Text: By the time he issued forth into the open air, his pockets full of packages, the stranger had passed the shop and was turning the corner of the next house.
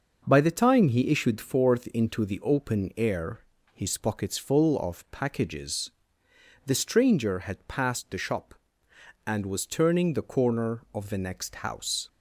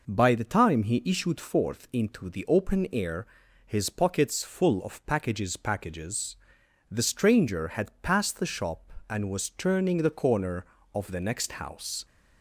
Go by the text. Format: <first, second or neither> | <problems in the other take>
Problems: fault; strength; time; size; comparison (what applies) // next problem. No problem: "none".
first | says "packages" twice; at 5.5 s